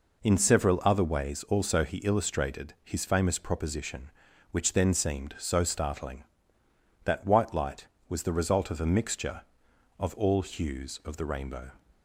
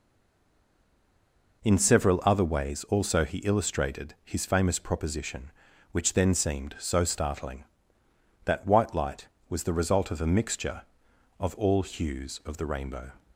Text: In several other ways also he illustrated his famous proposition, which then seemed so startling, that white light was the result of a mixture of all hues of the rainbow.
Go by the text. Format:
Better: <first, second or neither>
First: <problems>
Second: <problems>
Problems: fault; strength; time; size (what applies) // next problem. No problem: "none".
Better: first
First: none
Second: stays silent before the first word; noticeable; until 1.6 s; 1.6 s long